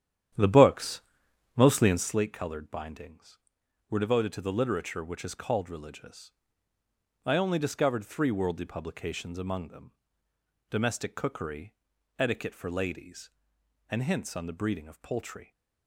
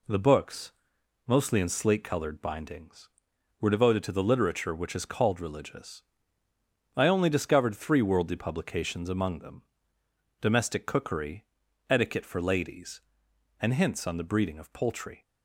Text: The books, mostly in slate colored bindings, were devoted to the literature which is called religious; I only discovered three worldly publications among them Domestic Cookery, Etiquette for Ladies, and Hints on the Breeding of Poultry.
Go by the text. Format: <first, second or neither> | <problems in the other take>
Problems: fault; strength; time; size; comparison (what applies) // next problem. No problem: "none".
second | starts louder than the rest; strong; until 2.2 s; 10.5 dB // pauses between "them" and "Domestic"; noticeable; at 9.9 s; 0.80 s long; noticeable in the second